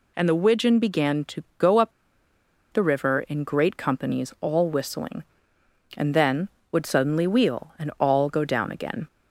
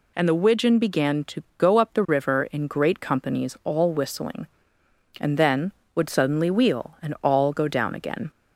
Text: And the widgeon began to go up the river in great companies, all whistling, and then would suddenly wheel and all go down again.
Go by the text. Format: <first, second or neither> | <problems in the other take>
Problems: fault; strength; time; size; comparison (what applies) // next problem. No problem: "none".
second | pauses between "up" and "the"; noticeable; at 1.9 s; 0.80 s long